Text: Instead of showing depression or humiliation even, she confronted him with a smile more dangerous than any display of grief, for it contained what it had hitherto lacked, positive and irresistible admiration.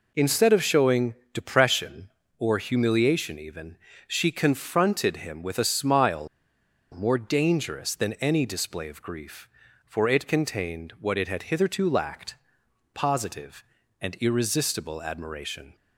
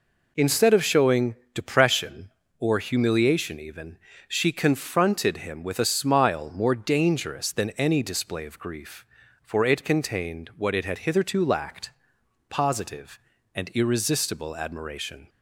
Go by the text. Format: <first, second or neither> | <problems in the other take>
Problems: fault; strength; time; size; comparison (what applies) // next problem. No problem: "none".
second | pauses between "showing" and "depression"; slight; at 1.1 s; 0.16 s long; slight in the second // pauses between "smile" and "more"; noticeable; at 6.2 s; 0.65 s long